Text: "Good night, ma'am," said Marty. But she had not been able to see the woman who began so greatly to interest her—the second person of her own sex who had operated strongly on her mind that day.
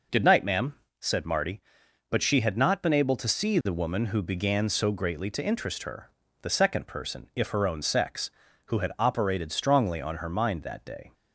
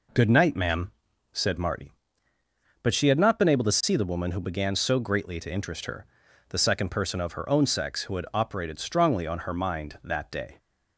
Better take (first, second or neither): second